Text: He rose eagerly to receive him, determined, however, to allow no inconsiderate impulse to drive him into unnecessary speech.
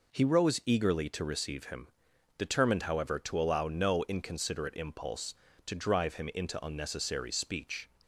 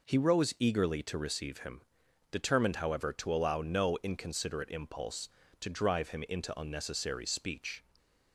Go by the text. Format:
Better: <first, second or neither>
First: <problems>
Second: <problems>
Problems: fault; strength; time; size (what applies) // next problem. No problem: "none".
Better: neither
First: none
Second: none